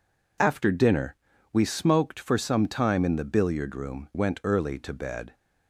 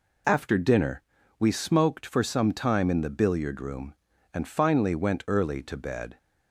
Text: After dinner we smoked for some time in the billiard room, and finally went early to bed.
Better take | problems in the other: second | pauses between "dinner" and "we"; slight; at 1.1 s; 0.36 s long; slight in the second // skips "and finally"; at 4.1 s

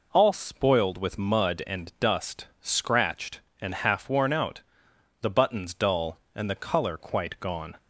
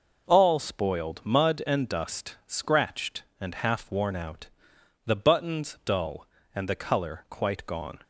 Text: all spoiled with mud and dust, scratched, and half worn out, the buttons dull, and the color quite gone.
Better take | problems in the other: first | skips "with"; at 1.2 s

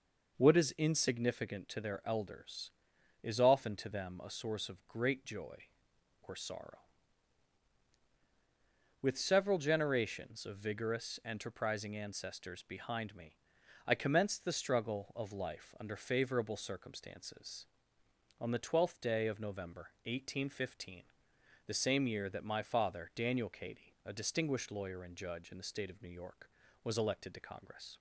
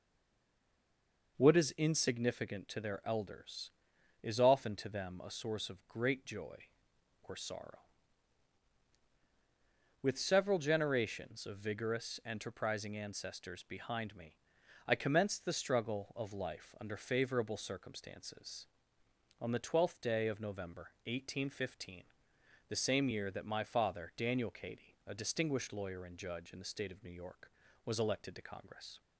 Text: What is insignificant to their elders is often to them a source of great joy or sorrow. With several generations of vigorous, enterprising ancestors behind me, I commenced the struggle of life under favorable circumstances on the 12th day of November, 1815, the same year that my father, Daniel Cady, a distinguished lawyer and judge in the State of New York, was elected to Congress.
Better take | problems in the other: first | stays silent before the first word; noticeable; until 1.3 s; 1.3 s long

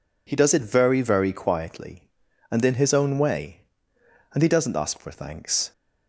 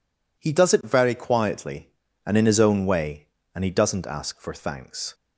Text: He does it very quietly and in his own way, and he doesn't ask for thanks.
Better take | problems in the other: second | says "very" twice; at 1.0 s

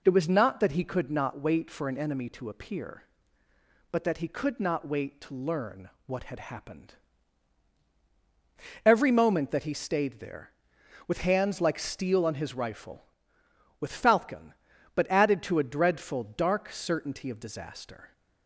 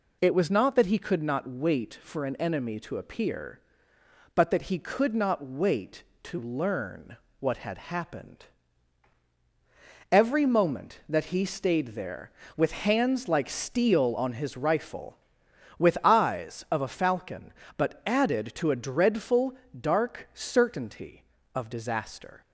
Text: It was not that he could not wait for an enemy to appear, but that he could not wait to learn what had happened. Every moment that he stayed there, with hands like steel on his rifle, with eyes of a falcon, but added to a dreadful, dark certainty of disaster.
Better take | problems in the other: second | pauses between "learn" and "what"; slight; at 5.8 s; 0.18 s long; slight in the second // skips "eyes of a"; at 13.9 s

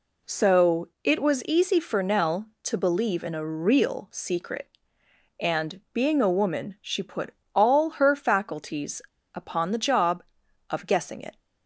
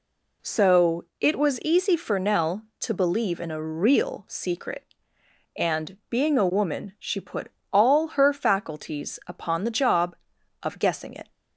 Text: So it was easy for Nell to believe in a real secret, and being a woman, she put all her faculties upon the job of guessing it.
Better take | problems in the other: second | pauses between "So" and "it"; slight; at 0.8 s; 0.16 s long; slight in the second // pauses between "put" and "all"; slight; at 7.3 s; 0.20 s long; slight in the second // pauses between "faculties" and "upon"; slight; at 9.0 s; 0.33 s long

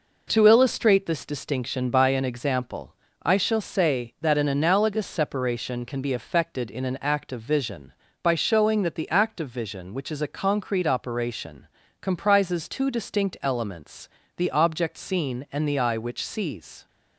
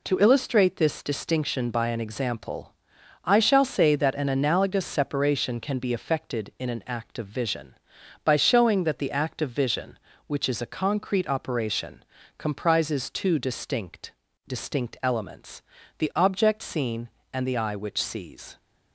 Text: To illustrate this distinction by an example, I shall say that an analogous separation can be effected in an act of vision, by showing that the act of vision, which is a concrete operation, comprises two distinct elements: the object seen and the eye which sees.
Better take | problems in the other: first | says "distinct" twice; at 14.4 s

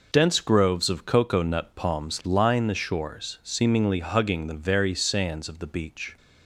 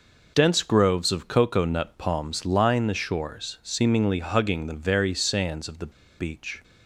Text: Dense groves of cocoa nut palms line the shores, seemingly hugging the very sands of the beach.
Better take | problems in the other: first | pauses between "the" and "beach"; slight; at 5.9 s; 0.28 s long

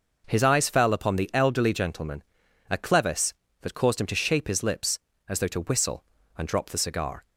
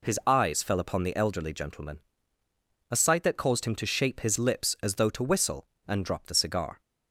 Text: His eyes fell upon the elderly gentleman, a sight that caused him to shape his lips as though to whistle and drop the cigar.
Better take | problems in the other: second | says "clevis" for "sight"; at 2.7 s

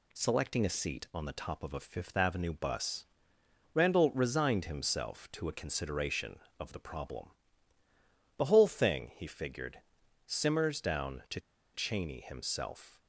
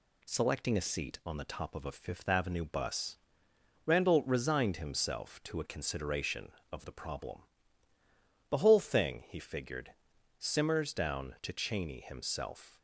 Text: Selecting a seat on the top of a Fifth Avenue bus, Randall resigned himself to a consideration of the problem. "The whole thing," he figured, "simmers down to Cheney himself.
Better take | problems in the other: second | pauses between "to" and "Cheney"; slight; at 11.3 s; 0.35 s long

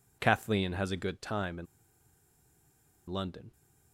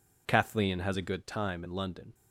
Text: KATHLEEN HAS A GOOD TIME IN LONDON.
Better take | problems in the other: second | pauses between "IN" and "LONDON"; strong; at 1.6 s; 1.4 s long

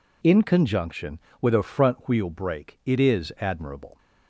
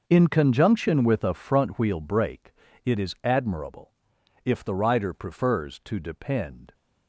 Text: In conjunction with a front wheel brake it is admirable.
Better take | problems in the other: first | pauses between "brake" and "it"; slight; at 2.5 s; 0.30 s long // goes on to say "If the rider prefers to depend"; strong; from 4.4 s on; 2.3 s long

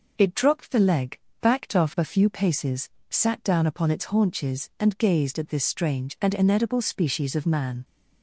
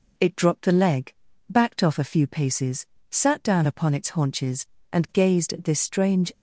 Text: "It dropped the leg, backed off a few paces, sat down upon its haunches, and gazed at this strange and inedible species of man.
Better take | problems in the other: first | stops before "and inedible species of man"; at 6.3 s

